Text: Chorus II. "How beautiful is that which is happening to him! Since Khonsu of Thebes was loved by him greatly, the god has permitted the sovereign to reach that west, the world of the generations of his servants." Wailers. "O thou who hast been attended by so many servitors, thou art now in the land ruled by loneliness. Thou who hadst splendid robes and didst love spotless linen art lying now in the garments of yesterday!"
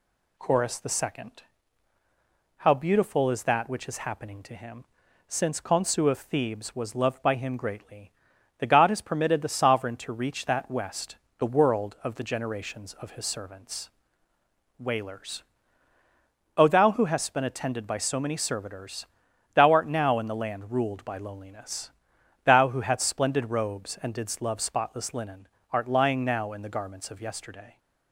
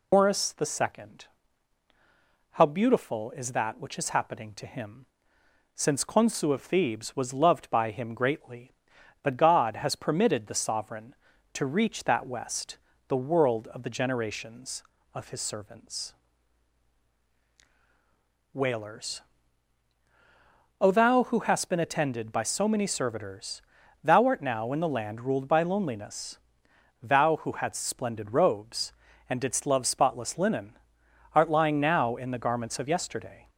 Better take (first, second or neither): first